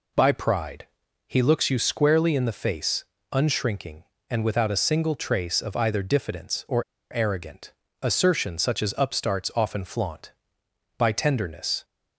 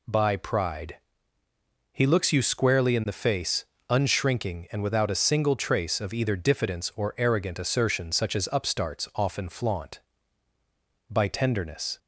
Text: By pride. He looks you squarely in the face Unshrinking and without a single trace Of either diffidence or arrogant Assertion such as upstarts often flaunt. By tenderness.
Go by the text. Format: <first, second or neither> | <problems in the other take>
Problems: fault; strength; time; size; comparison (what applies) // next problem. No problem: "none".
second | pauses between "face" and "Unshrinking"; slight; at 3.0 s; 0.28 s long; slight in the second // pauses between "or" and "arrogant"; slight; at 6.8 s; 0.29 s long // pauses between "arrogant" and "Assertion"; slight; at 7.7 s; 0.28 s long